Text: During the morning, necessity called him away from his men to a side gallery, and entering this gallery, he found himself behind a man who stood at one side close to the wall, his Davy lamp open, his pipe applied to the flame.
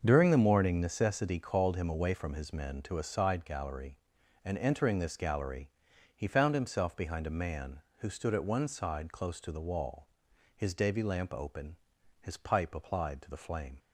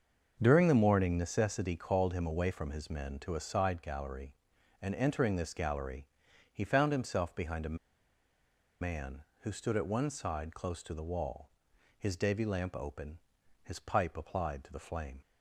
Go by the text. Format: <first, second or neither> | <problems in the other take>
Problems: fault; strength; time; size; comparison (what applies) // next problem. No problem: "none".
first | starts louder than the rest; until 1.4 s; 6.5 dB; also in the first // pauses between "a" and "man"; at 7.7 s; 1.0 s long